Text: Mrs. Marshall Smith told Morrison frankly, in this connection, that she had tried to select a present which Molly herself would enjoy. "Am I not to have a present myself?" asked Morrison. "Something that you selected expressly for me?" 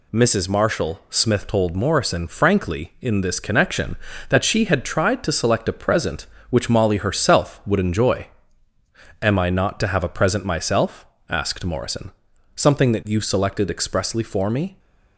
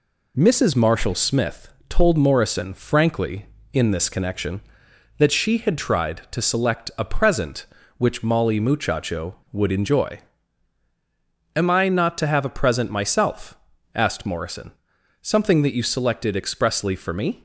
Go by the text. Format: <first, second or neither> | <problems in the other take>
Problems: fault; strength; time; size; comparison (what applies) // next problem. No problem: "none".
first | pauses between "Smith" and "told"; slight; at 1.6 s; 0.18 s long // says "muchacho" for "herself"; at 8.5 s